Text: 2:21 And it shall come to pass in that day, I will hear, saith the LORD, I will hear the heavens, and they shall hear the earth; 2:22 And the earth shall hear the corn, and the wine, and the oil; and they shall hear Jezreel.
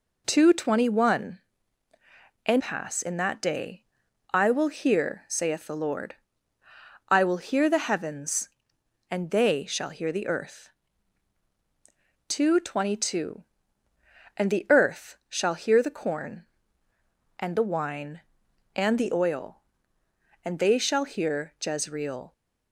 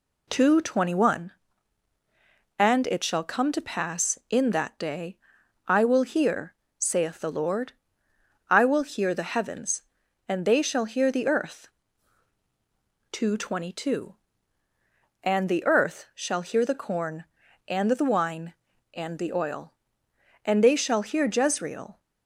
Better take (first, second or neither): second